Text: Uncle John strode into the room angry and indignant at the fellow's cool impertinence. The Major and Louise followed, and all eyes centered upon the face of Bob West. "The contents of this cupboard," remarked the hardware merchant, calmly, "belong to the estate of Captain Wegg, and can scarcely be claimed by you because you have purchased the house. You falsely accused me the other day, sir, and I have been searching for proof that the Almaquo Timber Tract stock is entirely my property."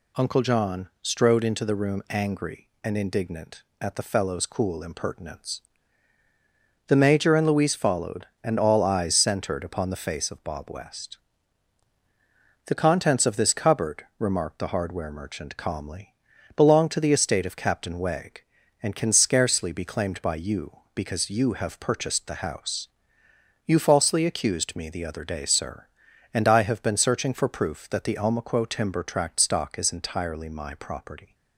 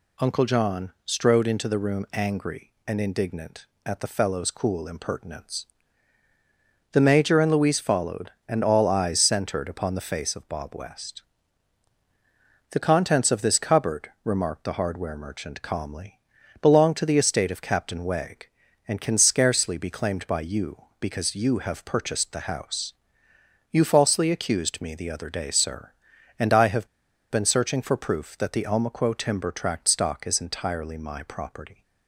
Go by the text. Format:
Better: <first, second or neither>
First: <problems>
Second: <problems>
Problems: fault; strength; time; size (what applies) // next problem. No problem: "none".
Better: first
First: none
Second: pauses between "have" and "been"; at 26.8 s; 0.43 s long